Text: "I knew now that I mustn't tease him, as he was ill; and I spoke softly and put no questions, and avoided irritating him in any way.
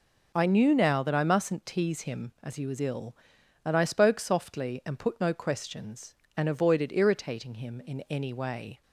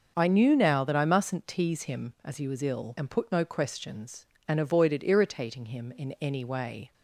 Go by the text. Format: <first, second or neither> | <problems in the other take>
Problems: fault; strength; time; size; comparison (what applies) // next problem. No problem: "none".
first | starts louder than the rest; until 1.1 s; 6.5 dB // skips "and I spoke softly"; at 2.9 s